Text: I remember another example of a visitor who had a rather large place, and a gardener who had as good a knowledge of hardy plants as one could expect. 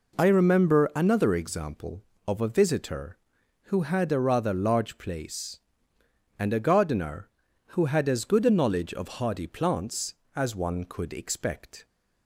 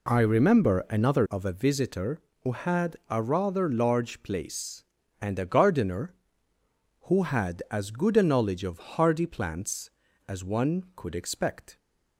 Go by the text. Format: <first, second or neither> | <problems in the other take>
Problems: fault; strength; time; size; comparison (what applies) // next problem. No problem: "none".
first | skips "example"; at 1.2 s